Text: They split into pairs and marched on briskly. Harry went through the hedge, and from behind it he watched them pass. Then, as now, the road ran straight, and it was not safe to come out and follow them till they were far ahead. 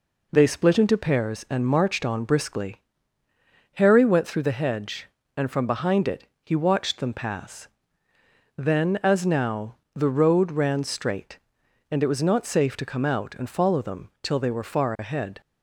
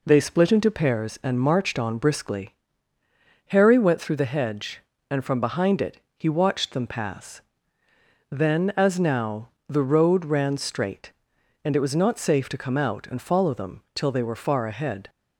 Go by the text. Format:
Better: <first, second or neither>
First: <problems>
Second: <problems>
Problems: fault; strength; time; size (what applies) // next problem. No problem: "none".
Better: neither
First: pauses between "it" and "he"; slight; at 6.2 s; 0.16 s long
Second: pauses between "it" and "he"; slight; at 6.0 s; 0.16 s long